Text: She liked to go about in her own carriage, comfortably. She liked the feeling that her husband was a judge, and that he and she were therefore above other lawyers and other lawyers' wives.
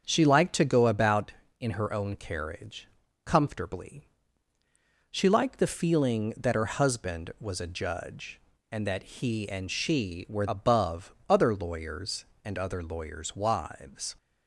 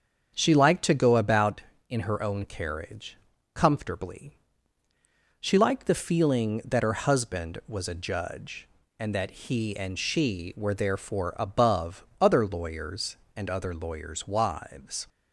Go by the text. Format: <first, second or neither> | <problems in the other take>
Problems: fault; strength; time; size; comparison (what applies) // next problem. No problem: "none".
second | starts louder than the rest; strong; until 1.0 s; 7.5 dB; strong in the second // skips "therefore"; at 10.4 s // pauses between "above" and "other"; slight; at 11.1 s; 0.16 s long; slight in the second